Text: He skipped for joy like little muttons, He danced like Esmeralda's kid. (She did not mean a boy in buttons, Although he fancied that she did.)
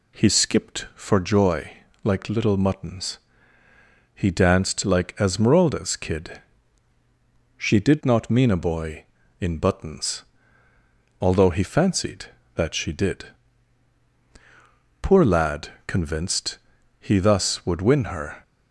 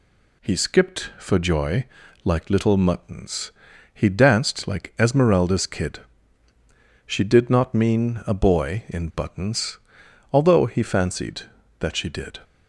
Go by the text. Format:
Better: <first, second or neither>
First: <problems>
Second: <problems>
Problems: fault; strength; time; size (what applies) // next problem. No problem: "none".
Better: second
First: pauses between "joy" and "like"; slight; at 1.7 s; 0.34 s long // goes on to say "Poor lad convinced he thus would win her"; strong; from 15.0 s on; 3.4 s long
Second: pauses between "joy" and "like"; at 1.8 s; 0.40 s long